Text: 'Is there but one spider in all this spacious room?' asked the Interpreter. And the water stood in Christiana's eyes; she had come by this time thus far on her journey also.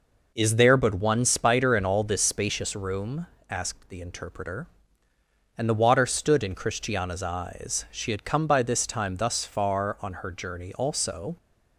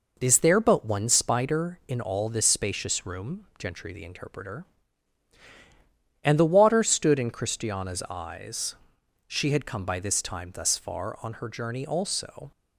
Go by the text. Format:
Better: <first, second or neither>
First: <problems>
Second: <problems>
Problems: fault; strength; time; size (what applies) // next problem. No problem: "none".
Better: first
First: none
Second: says "gentry" for "asked"; at 3.5 s